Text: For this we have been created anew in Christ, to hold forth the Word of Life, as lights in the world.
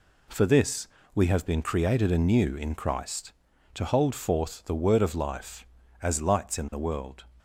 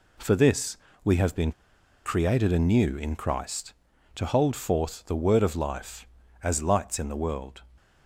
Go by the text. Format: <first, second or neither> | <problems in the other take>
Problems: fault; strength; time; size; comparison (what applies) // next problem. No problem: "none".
first | pauses between "this" and "we"; slight; at 0.7 s; 0.28 s long; slight in the first // pauses between "been" and "created"; noticeable; at 1.5 s; 0.52 s long